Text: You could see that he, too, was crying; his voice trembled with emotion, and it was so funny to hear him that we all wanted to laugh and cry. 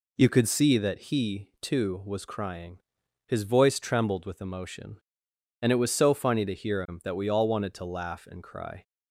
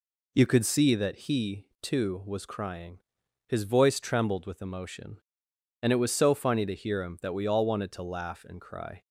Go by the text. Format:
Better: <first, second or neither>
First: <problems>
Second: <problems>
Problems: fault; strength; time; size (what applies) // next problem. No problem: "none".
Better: neither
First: none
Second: none